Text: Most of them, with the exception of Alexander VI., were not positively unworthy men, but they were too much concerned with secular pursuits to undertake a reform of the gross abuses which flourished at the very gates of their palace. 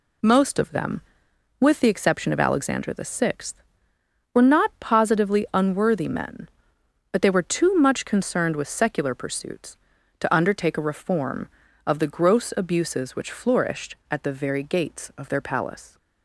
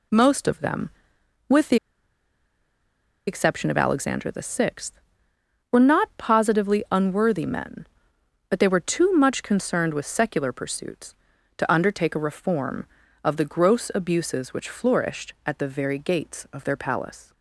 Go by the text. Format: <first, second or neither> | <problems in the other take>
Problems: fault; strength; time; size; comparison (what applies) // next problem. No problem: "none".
first | pauses between "the" and "exception"; strong; at 1.7 s; 1.5 s long